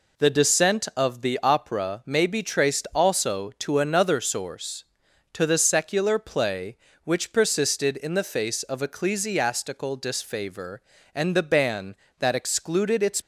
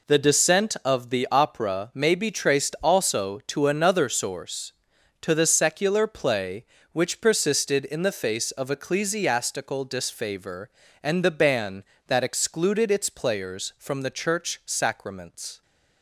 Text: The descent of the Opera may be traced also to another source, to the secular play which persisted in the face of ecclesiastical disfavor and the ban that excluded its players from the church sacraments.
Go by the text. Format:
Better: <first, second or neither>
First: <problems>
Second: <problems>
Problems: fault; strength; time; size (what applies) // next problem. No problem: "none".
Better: second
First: stops before "players from the church sacraments"; at 13.2 s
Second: none